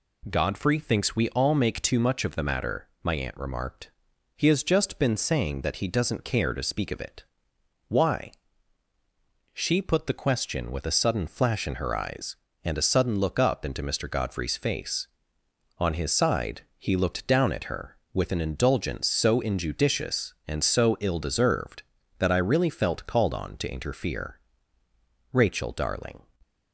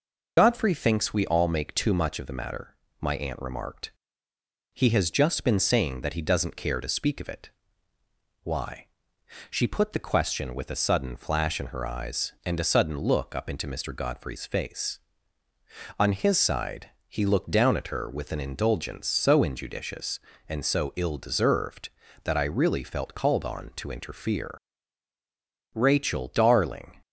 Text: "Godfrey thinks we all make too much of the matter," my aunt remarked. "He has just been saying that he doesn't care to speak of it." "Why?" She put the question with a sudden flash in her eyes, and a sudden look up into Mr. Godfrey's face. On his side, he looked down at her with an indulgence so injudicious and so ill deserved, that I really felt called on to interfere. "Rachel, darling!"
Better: first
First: none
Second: loses the start of "Godfrey"; at 0.3 s; 65 ms

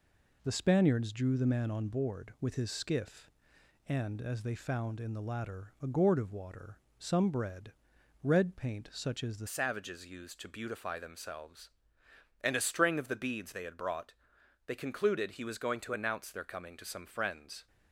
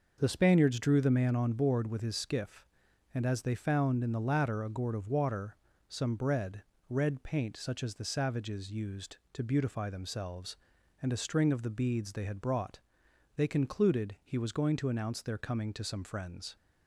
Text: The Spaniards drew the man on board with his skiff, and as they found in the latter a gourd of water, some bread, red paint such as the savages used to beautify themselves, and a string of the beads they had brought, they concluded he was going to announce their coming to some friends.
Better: second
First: changes voice at "savages"; from 9.4 s on; 8.2 s long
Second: none

